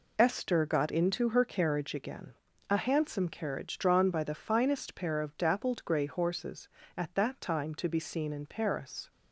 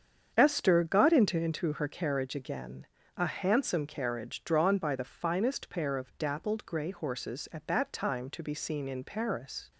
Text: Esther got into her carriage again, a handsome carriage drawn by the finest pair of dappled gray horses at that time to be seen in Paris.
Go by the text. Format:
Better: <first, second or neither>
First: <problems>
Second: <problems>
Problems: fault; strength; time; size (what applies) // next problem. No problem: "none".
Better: first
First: none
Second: starts louder than the rest; strong; until 1.3 s; 7.5 dB // says "into" twice; at 1.3 s